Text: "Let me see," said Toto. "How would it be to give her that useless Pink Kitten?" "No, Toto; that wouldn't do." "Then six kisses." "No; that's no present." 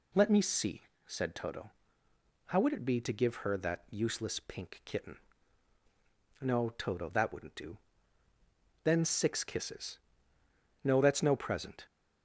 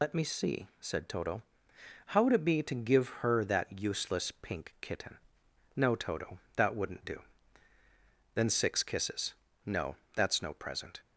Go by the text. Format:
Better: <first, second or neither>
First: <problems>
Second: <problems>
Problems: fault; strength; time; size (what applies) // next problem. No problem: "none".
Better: first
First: none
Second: loses the start of "Let"; at 0.0 s; 95 ms